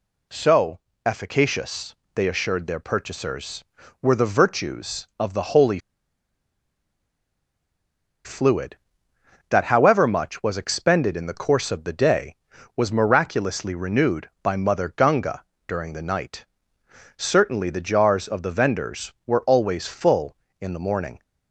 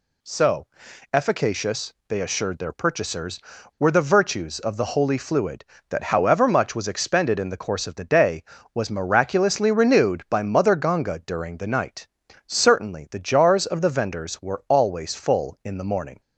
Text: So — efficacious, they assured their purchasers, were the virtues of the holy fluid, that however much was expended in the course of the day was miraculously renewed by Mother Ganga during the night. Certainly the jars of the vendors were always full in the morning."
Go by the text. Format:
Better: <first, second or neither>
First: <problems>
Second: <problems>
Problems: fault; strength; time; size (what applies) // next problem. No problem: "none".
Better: second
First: pauses between "holy" and "fluid"; strong; at 5.7 s; 2.4 s long // pauses between "Ganga" and "during"; slight; at 15.4 s; 0.22 s long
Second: none